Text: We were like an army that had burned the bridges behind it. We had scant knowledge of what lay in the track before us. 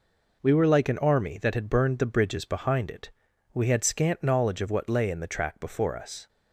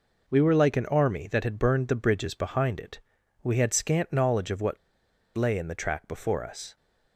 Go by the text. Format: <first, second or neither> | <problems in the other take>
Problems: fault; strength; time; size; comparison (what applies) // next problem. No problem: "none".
first | pauses between "what" and "lay"; noticeable; at 4.7 s; 0.59 s long